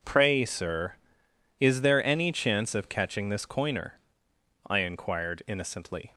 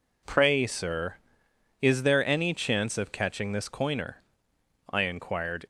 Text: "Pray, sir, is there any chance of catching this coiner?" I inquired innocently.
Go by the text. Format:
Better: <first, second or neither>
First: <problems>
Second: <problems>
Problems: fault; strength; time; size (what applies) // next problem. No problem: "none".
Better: first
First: none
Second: stops before "innocently"; at 5.6 s